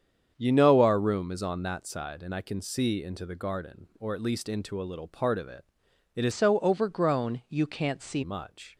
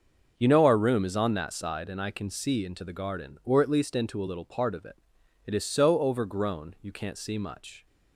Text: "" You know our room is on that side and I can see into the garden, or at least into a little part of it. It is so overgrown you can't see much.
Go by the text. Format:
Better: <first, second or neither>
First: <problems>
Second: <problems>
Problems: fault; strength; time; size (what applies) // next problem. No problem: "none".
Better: second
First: starts louder than the rest; strong; until 1.3 s; 7.5 dB // changes voice from "so" to "see"; from 6.3 to 8.2 s; 1.9 s long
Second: starts louder than the rest; until 1.3 s; 6.5 dB